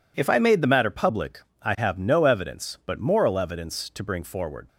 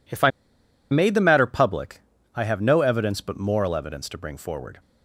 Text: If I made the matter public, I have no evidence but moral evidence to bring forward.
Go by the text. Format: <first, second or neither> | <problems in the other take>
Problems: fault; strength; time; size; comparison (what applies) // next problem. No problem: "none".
first | pauses between "I" and "made"; noticeable; at 0.2 s; 0.61 s long